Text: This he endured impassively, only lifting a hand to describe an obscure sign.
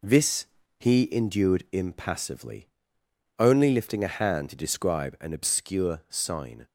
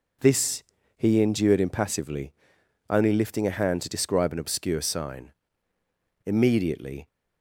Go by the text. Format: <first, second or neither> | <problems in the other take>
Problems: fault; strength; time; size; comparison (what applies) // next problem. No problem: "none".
first | pauses between "This" and "he"; slight; at 0.6 s; 0.34 s long; slight in the first // goes on to say "Immediately"; noticeable; from 6.2 s on; 0.82 s long